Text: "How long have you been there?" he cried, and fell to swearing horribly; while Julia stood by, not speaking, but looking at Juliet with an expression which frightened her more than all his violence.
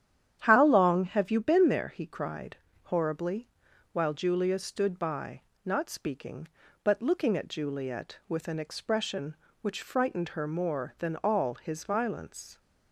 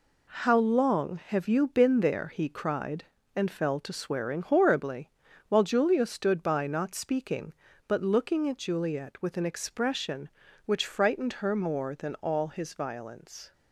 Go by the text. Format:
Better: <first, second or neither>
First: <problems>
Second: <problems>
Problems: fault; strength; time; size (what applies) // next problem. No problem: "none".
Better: second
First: starts louder than the rest; strong; until 1.4 s; 9.5 dB // skips "and fell to swearing"; at 2.6 s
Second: none